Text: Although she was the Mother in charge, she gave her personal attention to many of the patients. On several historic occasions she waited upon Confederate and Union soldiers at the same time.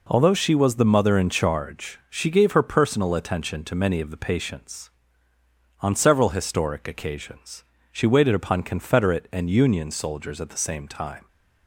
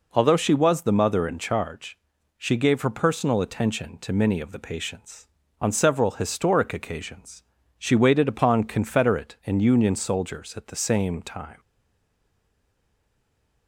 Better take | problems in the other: first | pauses between "occasions" and "she"; slight; at 7.4 s; 0.34 s long; slight in the first // stays silent after the last word; noticeable; from 11.5 s on; 2.1 s long

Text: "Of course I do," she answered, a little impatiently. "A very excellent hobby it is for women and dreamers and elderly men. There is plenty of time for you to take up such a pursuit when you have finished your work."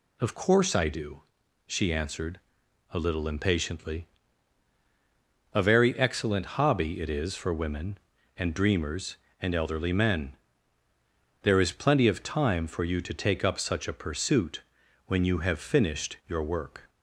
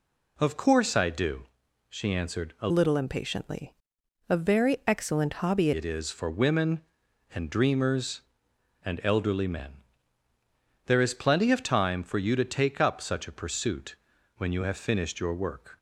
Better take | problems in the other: first | changes voice from "little" to "hobby"; from 2.6 to 5.7 s; 3.1 s long // pauses between "pursuit" and "when"; at 13.9 s; 0.42 s long; also in the first

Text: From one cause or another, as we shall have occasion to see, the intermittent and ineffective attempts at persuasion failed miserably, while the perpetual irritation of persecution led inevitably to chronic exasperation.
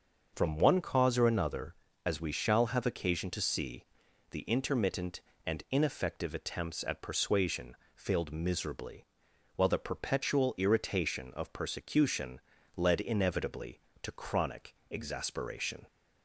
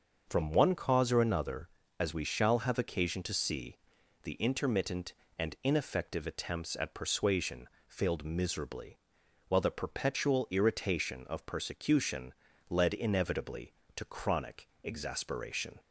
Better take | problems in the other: neither | starts louder than the rest; the same in both // pauses between "persuasion" and "failed"; slight; the same in both // pauses between "persecution" and "led"; slight; the same in both // pauses between "chronic" and "exasperation"; slight; the same in both

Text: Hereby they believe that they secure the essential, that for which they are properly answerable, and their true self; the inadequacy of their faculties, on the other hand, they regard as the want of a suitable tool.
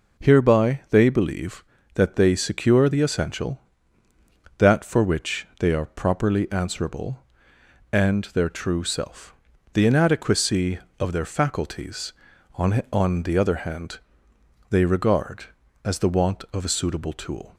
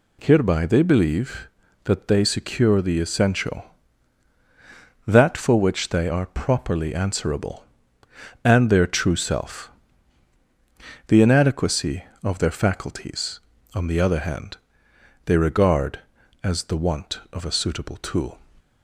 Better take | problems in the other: second | says "on" twice; at 12.9 s

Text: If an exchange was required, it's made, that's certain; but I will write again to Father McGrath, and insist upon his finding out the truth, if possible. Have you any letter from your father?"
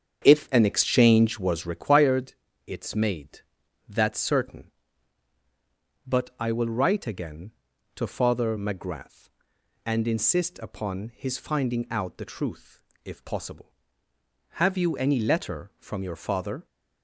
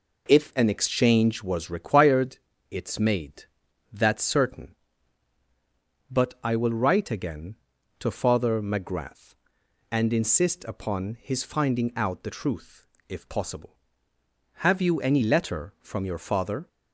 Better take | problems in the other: second | starts louder than the rest; strong; until 1.8 s; 8 dB

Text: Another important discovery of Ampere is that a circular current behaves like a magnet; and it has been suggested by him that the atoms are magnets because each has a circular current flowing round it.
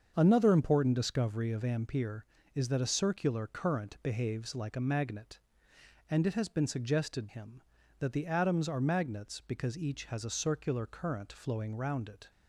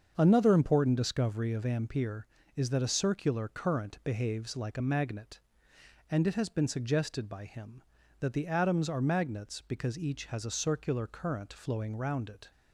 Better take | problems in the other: second | starts louder than the rest; until 1.1 s; 7 dB; also in the second // skips "by"; at 7.2 s

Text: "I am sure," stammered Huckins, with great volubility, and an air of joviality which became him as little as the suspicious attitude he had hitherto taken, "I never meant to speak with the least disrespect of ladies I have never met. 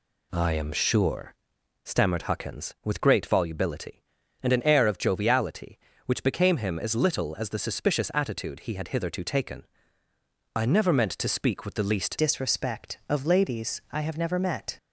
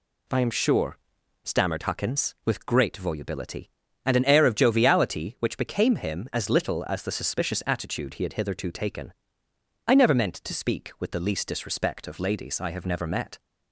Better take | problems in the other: second | changes voice at "disrespect"; from 12.1 s on; 2.6 s long

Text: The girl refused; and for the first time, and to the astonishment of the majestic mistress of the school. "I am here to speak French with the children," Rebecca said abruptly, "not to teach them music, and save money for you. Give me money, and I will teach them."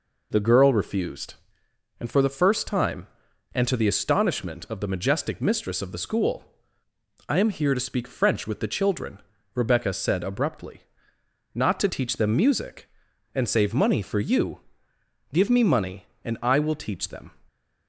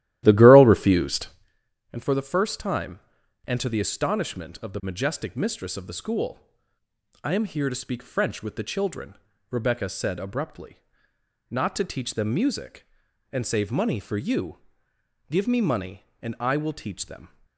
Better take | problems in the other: first | starts louder than the rest; strong; until 1.6 s; 13.5 dB

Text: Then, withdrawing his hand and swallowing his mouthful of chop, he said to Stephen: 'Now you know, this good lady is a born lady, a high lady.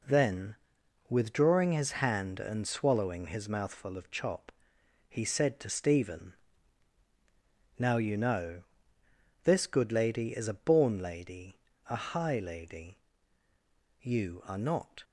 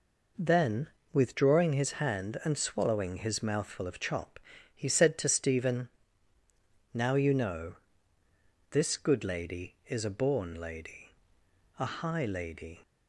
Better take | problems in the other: second | goes on to say "You are not"; noticeable; from 13.9 s on; 1.0 s long

